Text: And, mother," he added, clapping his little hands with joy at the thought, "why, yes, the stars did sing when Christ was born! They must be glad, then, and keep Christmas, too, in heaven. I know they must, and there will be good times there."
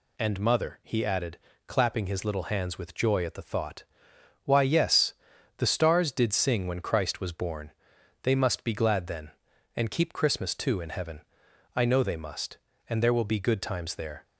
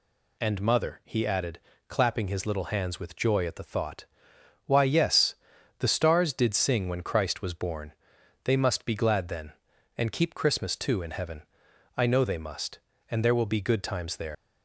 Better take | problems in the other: first | leaves "there" unfinished; at 14.3 s; 110 ms

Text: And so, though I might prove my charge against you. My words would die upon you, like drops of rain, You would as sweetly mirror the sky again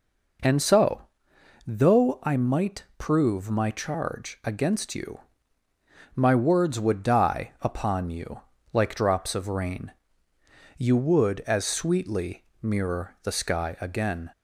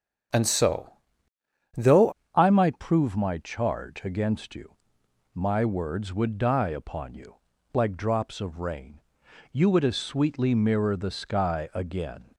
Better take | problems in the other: first | starts louder than the rest; strong; until 2.4 s; 8 dB // changes voice at "I"; from 2.3 s on; 10.0 s long

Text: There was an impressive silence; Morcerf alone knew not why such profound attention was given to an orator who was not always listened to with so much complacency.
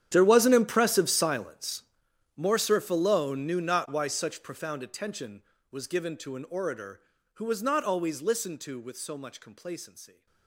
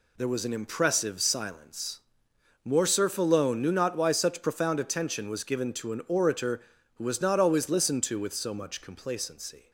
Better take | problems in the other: second | gets quieter; strong; throughout; 19 dB

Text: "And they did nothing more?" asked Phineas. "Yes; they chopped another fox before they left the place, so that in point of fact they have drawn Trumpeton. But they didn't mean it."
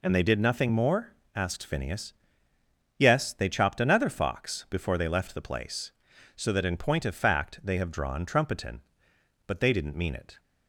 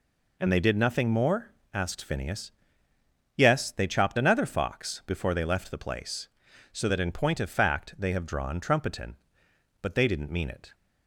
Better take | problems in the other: neither | none

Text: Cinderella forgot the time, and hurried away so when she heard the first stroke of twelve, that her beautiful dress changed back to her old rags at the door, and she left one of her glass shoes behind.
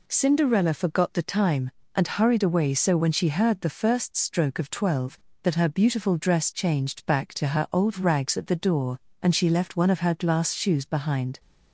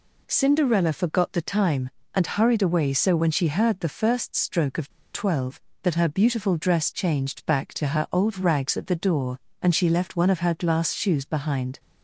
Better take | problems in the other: first | pauses between "of" and "twelve"; slight; at 4.8 s; 0.25 s long

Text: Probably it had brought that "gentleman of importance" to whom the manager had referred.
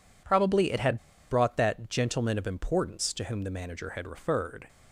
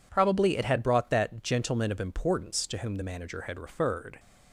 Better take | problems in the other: second | pauses between "had" and "brought"; slight; at 0.9 s; 0.34 s long

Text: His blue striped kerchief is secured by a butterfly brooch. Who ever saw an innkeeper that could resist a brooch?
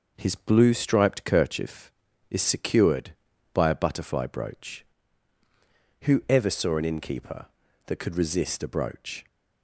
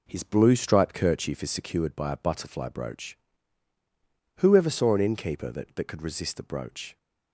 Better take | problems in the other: first | says "that" twice; at 5.7 s

